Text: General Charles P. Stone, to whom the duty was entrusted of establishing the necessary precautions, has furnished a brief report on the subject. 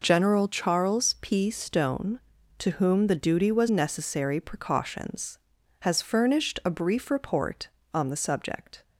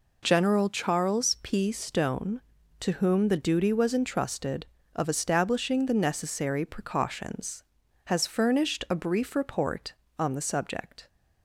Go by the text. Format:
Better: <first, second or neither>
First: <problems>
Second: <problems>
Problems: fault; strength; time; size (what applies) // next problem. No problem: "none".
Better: second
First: skips "entrusted of establishing the"; at 3.6 s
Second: none